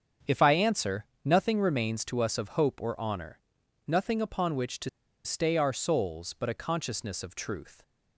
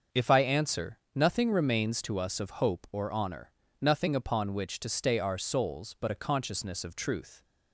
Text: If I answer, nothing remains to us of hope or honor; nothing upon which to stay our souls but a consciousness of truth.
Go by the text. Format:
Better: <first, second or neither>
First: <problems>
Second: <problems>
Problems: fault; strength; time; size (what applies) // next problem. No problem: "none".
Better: second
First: starts louder than the rest; strong; until 1.4 s; 7.5 dB // pauses between "to" and "stay"; slight; at 4.8 s; 0.35 s long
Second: starts louder than the rest; until 1.2 s; 6.5 dB